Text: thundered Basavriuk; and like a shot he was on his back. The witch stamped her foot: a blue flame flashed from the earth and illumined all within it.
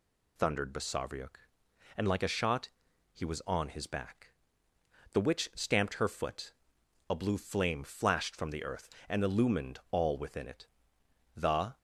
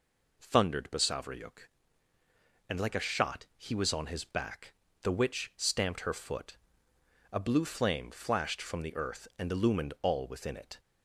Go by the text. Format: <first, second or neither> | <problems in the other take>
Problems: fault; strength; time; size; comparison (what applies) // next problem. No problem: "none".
second | pauses between "shot" and "he"; noticeable; at 2.6 s; 0.46 s long // goes on to say "The"; slight; from 11.3 s on; 0.40 s long